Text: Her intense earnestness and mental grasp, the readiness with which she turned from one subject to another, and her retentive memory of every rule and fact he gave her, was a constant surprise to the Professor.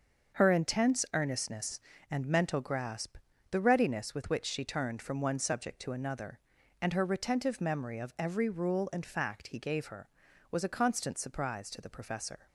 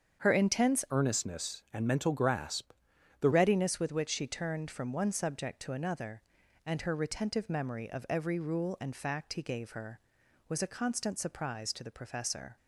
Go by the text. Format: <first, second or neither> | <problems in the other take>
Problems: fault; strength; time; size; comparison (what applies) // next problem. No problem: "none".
first | starts louder than the rest; strong; until 1.2 s; 7.5 dB; also in the first // changes voice from "earnestness" to "the"; from 0.9 to 3.3 s; 2.4 s long